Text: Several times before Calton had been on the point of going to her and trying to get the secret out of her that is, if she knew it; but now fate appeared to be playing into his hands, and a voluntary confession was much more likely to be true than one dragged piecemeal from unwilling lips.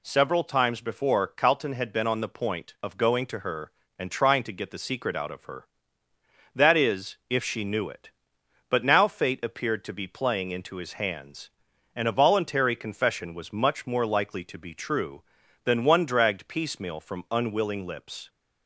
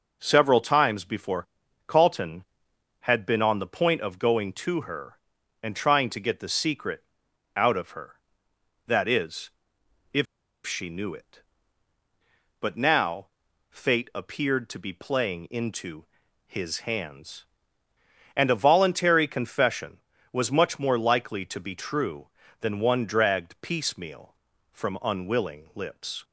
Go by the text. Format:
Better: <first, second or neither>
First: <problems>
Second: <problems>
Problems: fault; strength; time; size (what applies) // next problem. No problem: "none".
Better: first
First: none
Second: pauses between "before" and "Calton"; at 1.4 s; 0.40 s long // pauses between "secret" and "out"; noticeable; at 7.0 s; 0.52 s long // pauses between "if" and "she"; at 10.2 s; 0.40 s long // pauses between "now" and "fate"; at 13.2 s; 0.42 s long // pauses between "into" and "his"; at 16.0 s; 0.40 s long